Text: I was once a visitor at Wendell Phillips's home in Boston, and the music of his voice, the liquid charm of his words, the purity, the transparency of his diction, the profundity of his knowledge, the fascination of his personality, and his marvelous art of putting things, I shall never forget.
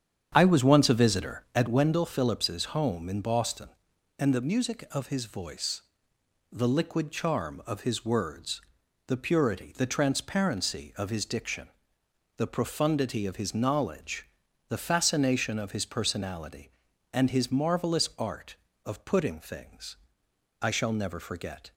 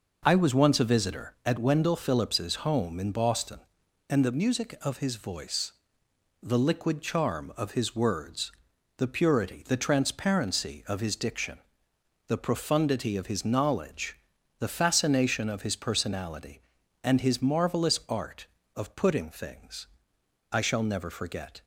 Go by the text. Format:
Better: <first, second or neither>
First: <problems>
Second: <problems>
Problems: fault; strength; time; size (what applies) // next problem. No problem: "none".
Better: second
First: starts louder than the rest; strong; until 1.8 s; 8 dB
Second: none